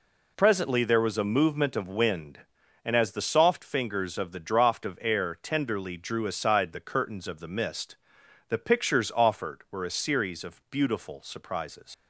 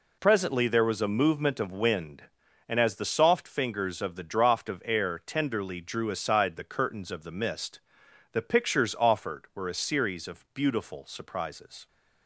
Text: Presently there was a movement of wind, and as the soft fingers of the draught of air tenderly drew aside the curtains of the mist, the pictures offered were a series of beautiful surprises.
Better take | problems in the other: second | leaves "surprises" unfinished; at 11.9 s; 90 ms

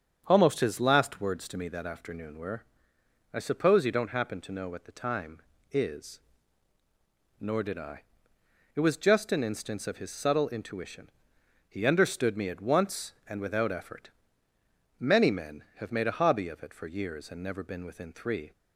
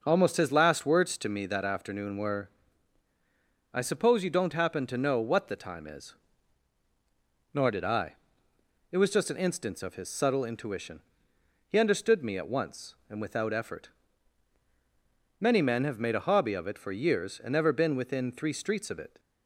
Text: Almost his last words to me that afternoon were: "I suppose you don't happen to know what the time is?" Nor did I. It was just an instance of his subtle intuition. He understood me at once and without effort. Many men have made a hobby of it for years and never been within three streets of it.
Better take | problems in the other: second | starts louder than the rest; strong; until 1.2 s; 8 dB; also in the second // stops before "streets of it"; at 18.5 s

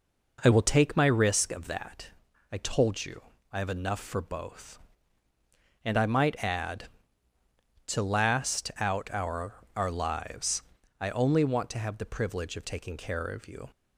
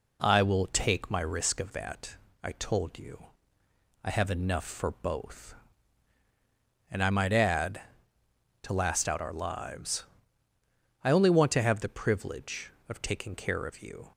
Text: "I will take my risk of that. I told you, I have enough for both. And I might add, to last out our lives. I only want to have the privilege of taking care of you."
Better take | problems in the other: second | says "our" twice; at 9.7 s

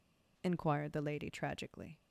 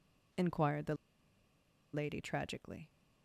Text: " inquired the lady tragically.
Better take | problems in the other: first | pauses between "the" and "lady"; at 0.9 s; 0.99 s long

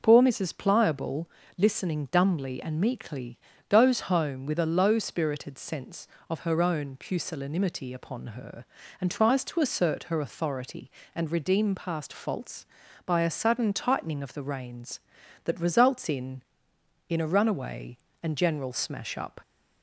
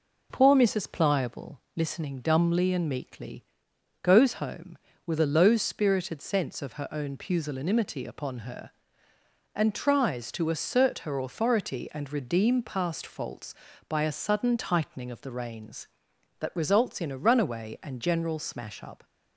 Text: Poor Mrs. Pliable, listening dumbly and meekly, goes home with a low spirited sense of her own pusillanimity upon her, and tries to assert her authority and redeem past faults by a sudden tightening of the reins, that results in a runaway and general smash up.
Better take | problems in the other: second | says "in" twice; at 17.0 s

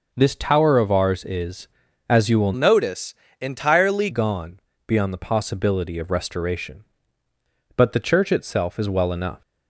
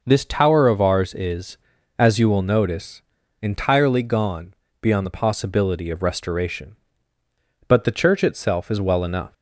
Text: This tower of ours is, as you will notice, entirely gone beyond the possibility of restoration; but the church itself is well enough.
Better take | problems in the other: second | changes voice from "notice" to "entirely"; from 2.5 to 4.0 s; 1.5 s long // pauses between "gone" and "beyond"; slight; at 4.5 s; 0.28 s long; slight in the second

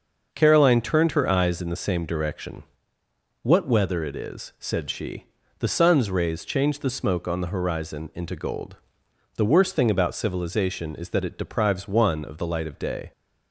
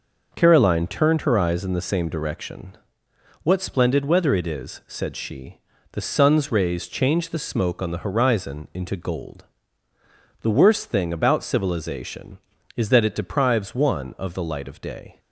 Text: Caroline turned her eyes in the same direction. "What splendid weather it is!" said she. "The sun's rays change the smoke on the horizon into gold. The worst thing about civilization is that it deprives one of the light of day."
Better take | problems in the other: second | starts louder than the rest; until 1.3 s; 6 dB // skips "splendid"; at 3.6 s

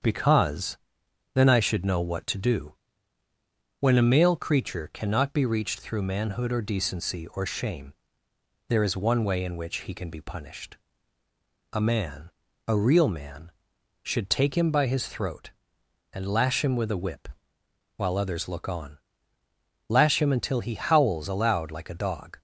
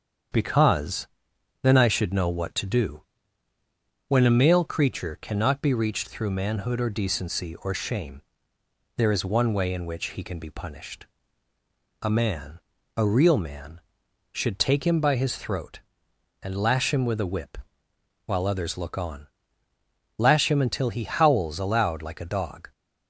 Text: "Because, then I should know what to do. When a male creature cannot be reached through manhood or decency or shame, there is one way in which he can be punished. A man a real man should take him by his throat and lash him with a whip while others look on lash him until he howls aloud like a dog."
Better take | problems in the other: neither | starts louder than the rest; strong; the same in both // pauses between "man" and "a"; the same in both // pauses between "whip" and "while"; noticeable; the same in both // pauses between "on" and "lash"; noticeable; the same in both

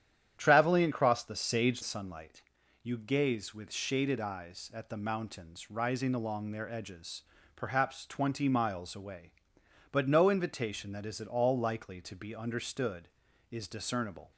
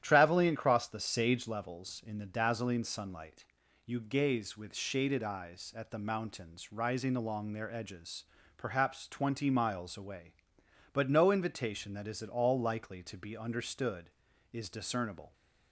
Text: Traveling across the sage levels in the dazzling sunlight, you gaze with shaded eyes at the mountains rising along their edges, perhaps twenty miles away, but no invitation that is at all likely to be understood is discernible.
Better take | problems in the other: second | starts louder than the rest; strong; until 1.3 s; 10 dB; strong in the second // skips "levels in the dazzling"; at 1.8 s

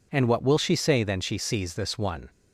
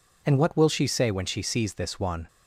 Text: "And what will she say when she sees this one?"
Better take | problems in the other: second | says "then" for "when"; at 1.0 s

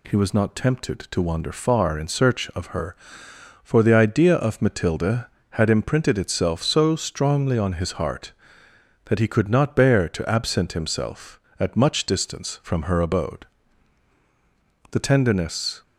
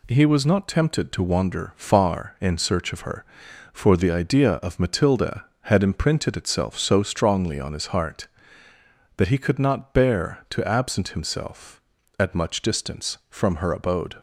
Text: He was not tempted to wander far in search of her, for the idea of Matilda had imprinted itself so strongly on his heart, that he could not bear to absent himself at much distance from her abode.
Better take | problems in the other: second | goes on to say "The tenderness"; noticeable; from 14.8 s on; 0.92 s long

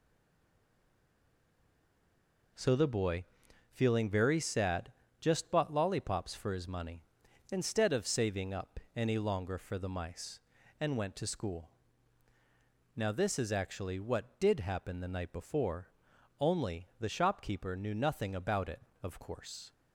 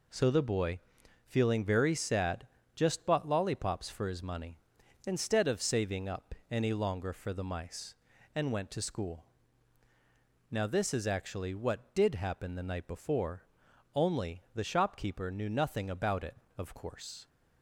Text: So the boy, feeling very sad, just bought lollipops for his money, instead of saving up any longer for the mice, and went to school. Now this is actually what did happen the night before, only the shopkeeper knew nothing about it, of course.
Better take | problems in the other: second | stays silent before the first word; strong; until 2.5 s; 2.5 s long // pauses between "up" and "any"; slight; at 8.7 s; 0.18 s long; slight in the second

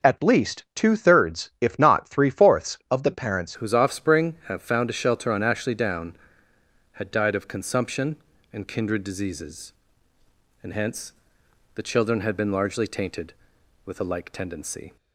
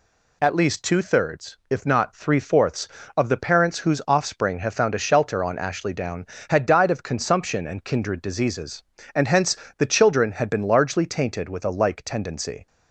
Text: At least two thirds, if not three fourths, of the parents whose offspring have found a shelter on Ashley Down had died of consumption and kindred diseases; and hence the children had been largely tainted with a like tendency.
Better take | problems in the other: second | changes voice at "whose"; from 3.5 s on; 11.4 s long // pauses between "hence" and "the"; noticeable; at 11.1 s; 0.64 s long; slight in the second

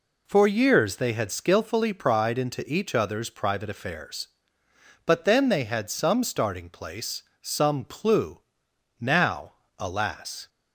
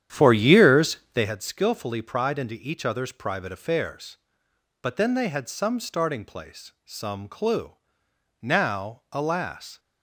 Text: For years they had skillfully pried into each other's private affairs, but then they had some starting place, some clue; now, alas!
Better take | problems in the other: first | starts louder than the rest; strong; until 1.3 s; 10 dB // pauses between "years" and "they"; slight; at 0.9 s; 0.16 s long

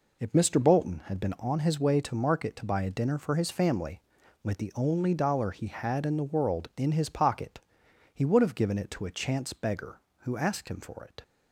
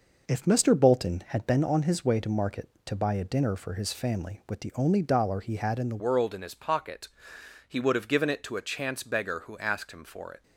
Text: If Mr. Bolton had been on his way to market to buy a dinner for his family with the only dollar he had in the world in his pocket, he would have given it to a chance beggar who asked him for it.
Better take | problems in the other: first | changes voice at "world"; from 6.0 s on; 4.4 s long

